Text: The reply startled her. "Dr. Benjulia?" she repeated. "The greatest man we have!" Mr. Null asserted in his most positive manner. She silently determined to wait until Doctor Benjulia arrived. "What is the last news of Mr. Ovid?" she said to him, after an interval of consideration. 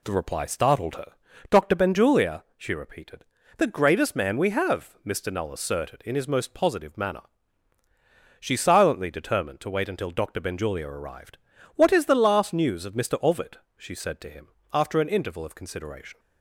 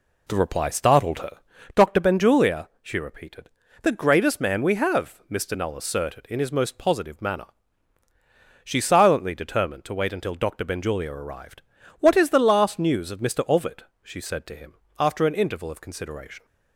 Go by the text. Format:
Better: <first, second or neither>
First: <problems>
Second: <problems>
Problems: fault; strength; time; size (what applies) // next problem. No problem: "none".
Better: first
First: none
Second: starts louder than the rest; slight; until 1.7 s; 2.5 dB